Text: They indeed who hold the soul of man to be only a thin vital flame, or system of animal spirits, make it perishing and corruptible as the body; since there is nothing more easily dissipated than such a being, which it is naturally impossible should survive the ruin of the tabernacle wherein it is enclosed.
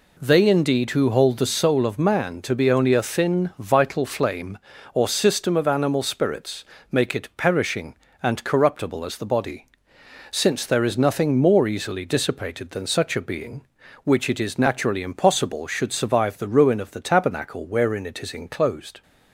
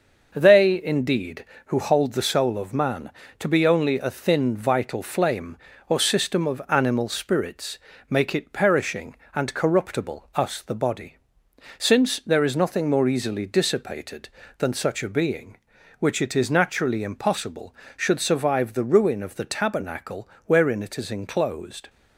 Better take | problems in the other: first | says "us" for "as"; at 10.3 s // pauses between "tabernacle" and "wherein"; slight; at 20.2 s; 0.16 s long

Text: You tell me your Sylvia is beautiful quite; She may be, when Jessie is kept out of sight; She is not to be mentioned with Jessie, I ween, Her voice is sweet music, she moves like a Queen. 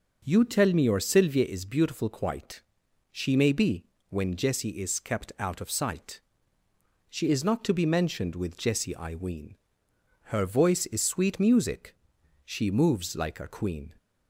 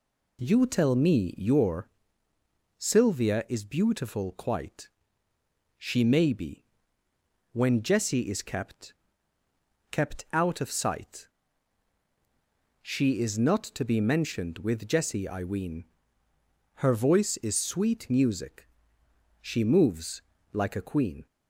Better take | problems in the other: first | pauses between "your" and "Sylvia"; noticeable; at 1.8 s; 0.88 s long // says "kept" twice; at 9.9 s // pauses between "moves" and "like"; slight; at 20.2 s; 0.32 s long

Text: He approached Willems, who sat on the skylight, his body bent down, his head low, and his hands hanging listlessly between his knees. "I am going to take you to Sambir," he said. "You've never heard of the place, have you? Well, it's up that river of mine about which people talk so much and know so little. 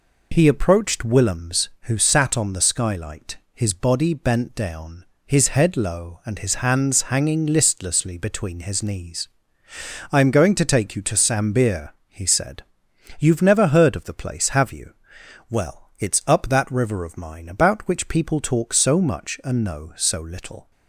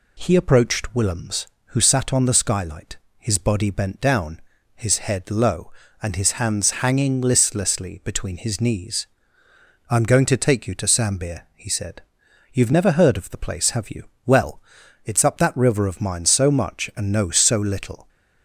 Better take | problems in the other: first | skips "about which people talk"; at 16.2 s

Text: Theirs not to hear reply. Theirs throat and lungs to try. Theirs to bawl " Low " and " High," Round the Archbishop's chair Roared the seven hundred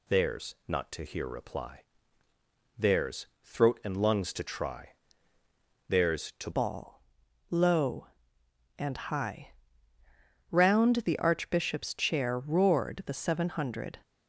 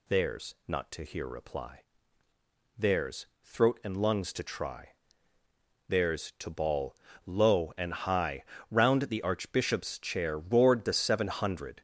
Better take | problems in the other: second | pauses between "Theirs" and "throat"; slight; at 3.2 s; 0.18 s long; slight in the second // changes voice at "bawl"; from 6.5 s on; 7.4 s long

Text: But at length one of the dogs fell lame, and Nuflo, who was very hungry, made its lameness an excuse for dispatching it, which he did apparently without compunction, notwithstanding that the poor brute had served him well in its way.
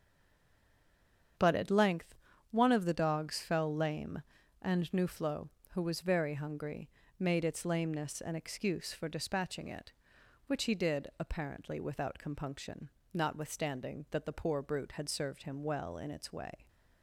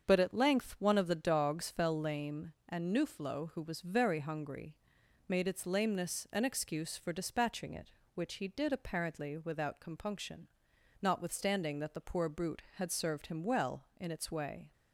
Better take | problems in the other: second | stays silent before the first word; noticeable; until 1.3 s; 1.3 s long // starts louder than the rest; strong; until 2.7 s; 7.5 dB; also in the second // pauses between "length" and "one"; slight; at 2.1 s; 0.34 s long

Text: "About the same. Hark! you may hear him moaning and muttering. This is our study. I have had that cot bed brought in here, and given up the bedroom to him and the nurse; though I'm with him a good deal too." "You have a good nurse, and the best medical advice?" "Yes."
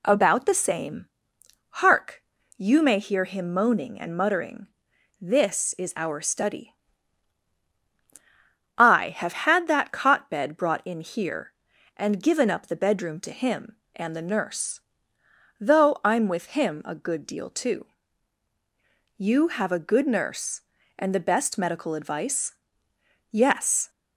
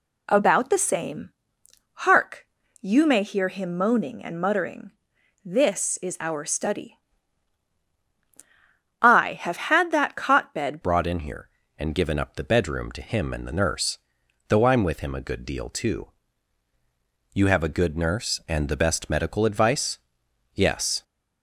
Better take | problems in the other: first | changes voice at "brought"; from 10.8 s on; 10.2 s long

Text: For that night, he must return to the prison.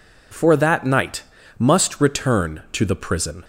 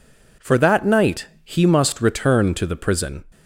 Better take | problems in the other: second | skips "he"; at 1.4 s

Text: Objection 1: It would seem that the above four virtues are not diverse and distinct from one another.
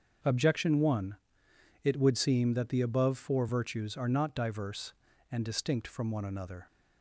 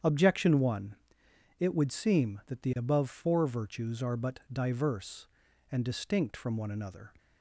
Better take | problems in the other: first | starts louder than the rest; strong; until 1.6 s; 8.5 dB; also in the first // says "but" for "not"; at 4.1 s

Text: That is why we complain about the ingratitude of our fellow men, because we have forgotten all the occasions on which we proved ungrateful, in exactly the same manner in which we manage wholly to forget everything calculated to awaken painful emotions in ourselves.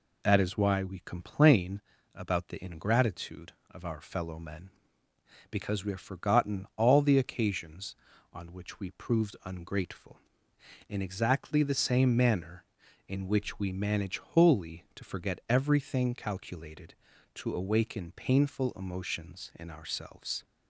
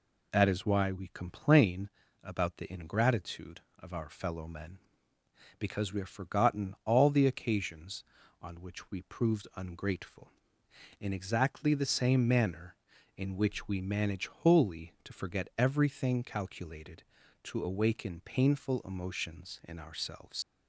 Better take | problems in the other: first | pauses between "complain" and "about"; slight; at 1.8 s; 0.34 s long; slight in the first // leaves "ourselves" unfinished; at 20.4 s; 105 ms

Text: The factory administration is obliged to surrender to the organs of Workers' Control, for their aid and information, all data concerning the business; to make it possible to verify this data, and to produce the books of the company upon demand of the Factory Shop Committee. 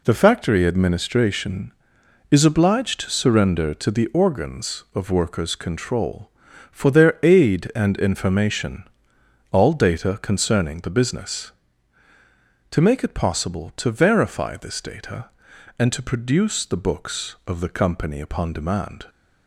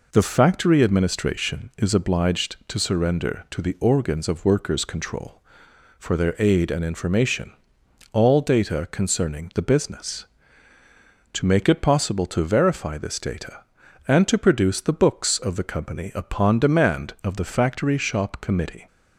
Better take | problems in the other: second | stops before "of the Factory Shop Committee"; at 19.0 s

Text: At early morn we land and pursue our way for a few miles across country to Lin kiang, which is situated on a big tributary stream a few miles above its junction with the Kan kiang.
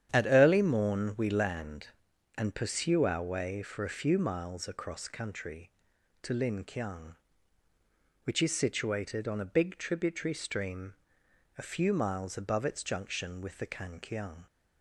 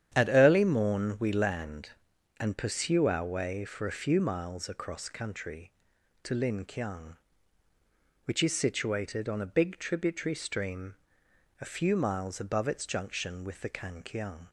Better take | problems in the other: neither | starts louder than the rest; strong; the same in both // pauses between "stream" and "a"; noticeable; the same in both

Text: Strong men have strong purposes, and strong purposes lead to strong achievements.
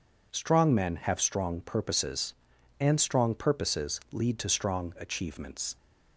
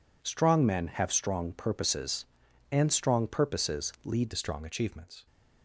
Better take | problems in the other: first | changes voice at "to"; from 4.2 s on; 1.0 s long

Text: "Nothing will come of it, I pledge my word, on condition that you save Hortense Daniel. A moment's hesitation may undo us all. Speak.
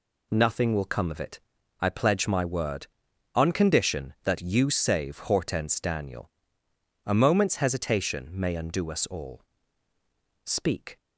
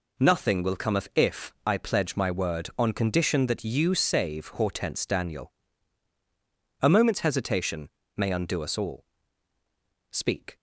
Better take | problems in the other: first | says "if" for "it"; at 1.1 s // pauses between "hesitation" and "may"; slight; at 7.8 s; 0.26 s long

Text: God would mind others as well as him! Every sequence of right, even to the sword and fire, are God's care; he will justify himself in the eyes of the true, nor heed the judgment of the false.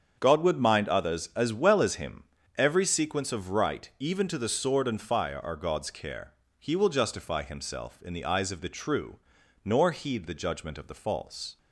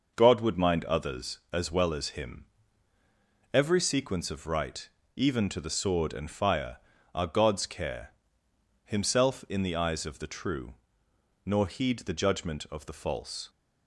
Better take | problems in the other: first | starts louder than the rest; noticeable; until 1.1 s; 6 dB; also in the first // skips "he will justify"; at 8.4 s

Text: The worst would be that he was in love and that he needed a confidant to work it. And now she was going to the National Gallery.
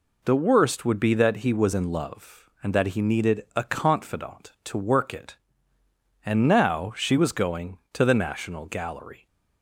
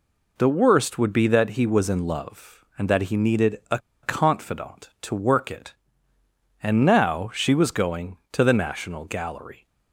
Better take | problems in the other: first | pauses between "a" and "confidant"; slight; at 3.7 s; 0.25 s long

